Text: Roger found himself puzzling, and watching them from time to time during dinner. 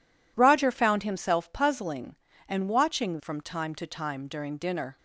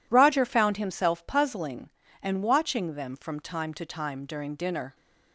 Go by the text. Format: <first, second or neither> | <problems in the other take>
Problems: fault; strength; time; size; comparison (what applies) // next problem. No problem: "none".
second | skips "them"; at 3.1 s